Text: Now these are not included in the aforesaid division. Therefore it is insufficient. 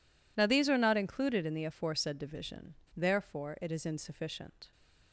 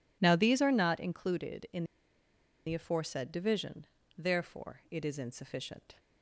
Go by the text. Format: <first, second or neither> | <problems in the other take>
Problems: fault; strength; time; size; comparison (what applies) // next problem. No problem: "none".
first | pauses between "in" and "the"; noticeable; at 1.8 s; 0.82 s long